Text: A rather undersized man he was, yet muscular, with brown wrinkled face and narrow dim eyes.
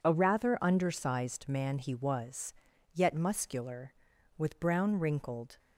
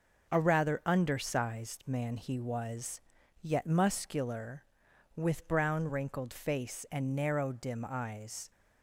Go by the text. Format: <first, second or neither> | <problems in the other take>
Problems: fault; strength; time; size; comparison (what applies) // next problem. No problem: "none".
second | stops before "face and narrow dim eyes"; at 5.5 s